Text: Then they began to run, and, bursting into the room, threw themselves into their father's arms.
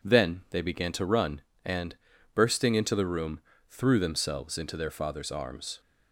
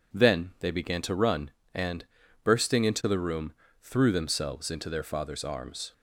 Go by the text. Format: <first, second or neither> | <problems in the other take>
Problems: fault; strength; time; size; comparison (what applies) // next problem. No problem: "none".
neither | none